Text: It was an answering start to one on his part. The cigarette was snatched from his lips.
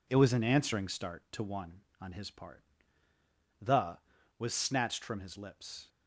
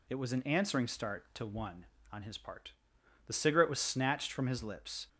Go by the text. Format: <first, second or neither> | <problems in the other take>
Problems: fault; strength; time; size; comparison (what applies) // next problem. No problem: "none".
second | skips "cigarette"; at 4.1 s